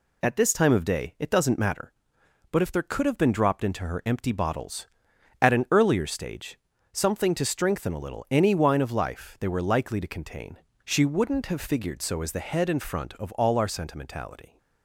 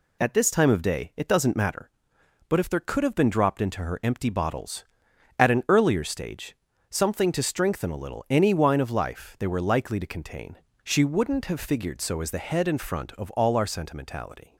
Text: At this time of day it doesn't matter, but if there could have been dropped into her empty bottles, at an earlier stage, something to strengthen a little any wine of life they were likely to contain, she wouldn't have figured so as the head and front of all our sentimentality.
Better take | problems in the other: neither | none

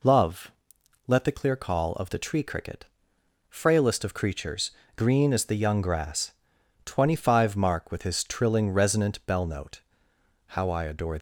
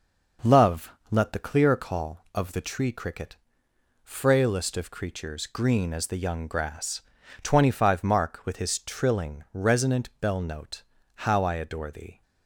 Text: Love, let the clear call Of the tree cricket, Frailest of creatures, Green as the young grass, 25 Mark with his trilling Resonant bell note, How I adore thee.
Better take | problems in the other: second | stops before "thee"; at 11.1 s

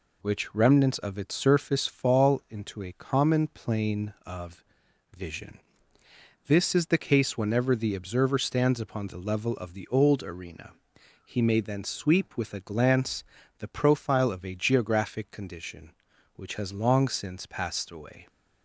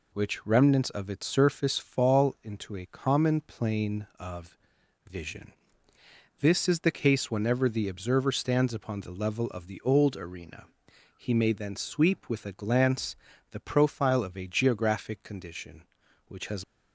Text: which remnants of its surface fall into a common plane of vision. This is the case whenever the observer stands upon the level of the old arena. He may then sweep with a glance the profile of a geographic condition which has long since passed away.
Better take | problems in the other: first | pauses between "of" and "vision"; noticeable; at 4.5 s; 0.54 s long; noticeable in the first // pauses between "glance" and "the"; slight; at 13.1 s; 0.36 s long; slight in the first // stops before "long since passed away"; at 16.6 s

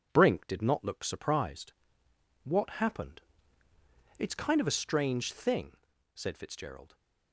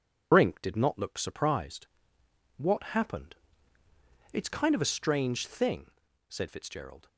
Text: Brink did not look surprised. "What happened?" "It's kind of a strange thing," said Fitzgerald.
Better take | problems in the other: first | loses the start of "Brink"; at 0.3 s; 60 ms

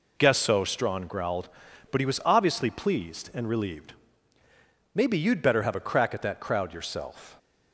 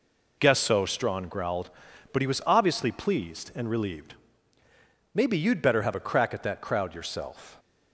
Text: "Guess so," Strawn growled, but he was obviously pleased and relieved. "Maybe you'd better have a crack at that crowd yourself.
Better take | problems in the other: neither | none

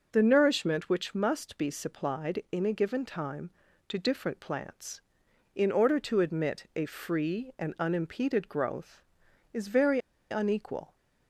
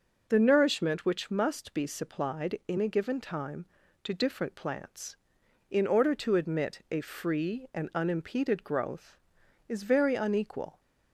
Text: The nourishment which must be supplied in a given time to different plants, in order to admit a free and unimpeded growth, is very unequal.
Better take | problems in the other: second | pauses between "very" and "unequal"; slight; at 9.9 s; 0.32 s long

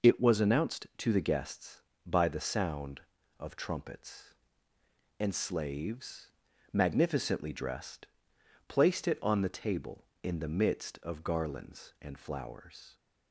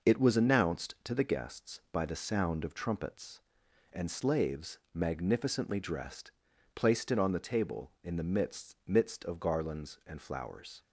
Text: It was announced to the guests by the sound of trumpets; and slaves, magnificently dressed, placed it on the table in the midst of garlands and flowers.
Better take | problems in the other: first | says "midst" twice; at 8.8 s

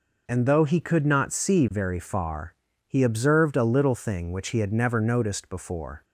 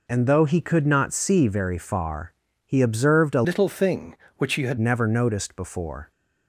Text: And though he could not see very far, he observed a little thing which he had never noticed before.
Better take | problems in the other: first | changes voice from "little" to "had"; from 3.4 to 4.7 s; 1.3 s long

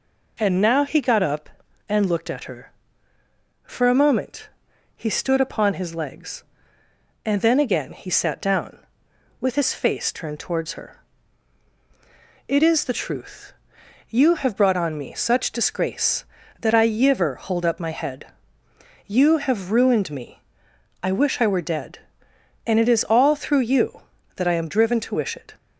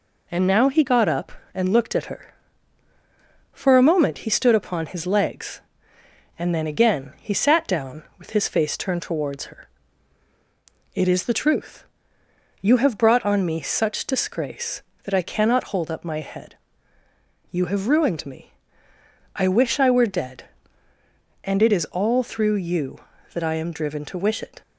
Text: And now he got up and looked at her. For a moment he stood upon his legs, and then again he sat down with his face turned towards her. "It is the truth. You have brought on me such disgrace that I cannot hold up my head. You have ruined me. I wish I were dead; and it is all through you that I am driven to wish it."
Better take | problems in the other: second | pauses between "moment" and "he"; noticeable; at 4.4 s; 0.48 s long // says "yiver" for "cannot"; at 16.8 s

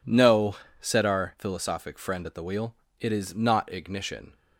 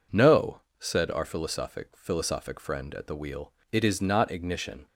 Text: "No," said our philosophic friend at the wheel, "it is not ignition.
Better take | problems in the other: first | says "philosophic" twice; at 1.9 s

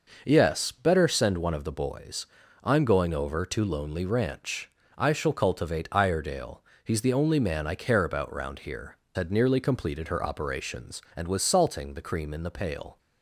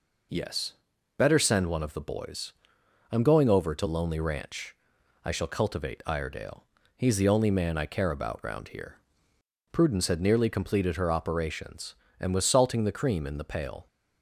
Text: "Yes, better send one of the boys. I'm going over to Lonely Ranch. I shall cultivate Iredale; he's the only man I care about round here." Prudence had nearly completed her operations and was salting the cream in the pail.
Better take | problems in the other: second | skips "Prudence"; at 9.0 s

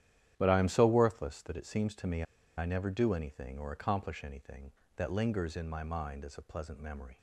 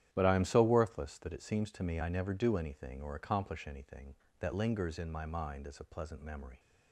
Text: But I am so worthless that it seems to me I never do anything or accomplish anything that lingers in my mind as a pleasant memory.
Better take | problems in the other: second | starts louder than the rest; strong; until 1.3 s; 11 dB; strong in the second // pauses between "me" and "I"; slight; at 2.2 s; 0.34 s long

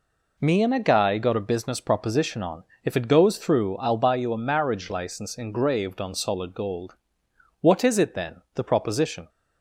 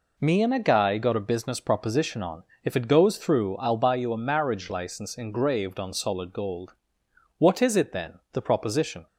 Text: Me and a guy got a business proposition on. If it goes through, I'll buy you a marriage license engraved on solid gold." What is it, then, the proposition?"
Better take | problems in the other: neither | none

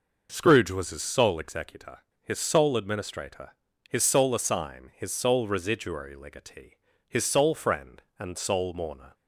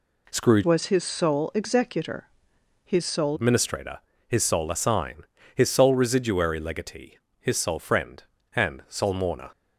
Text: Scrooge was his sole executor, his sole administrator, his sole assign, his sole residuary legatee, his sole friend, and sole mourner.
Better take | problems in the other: first | changes voice from "was" to "sole"; from 0.6 to 3.3 s; 2.7 s long

